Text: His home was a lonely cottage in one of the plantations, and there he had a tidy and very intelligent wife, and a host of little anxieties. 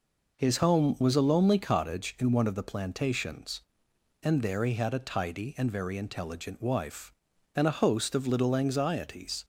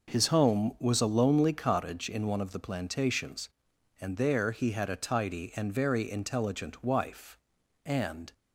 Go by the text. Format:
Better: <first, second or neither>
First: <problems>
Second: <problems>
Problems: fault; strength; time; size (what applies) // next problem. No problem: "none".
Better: first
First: none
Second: stops before "a host of little anxieties"; at 8.3 s